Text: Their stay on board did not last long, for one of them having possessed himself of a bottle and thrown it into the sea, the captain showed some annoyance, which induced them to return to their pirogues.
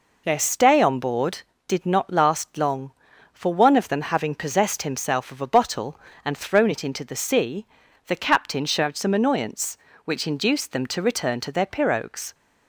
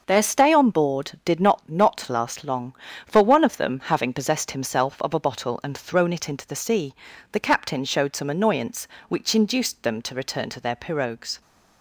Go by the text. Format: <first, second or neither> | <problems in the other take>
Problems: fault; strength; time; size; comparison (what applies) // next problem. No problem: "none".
first | starts louder than the rest; until 1.0 s; 6 dB // says "not" twice; at 1.6 s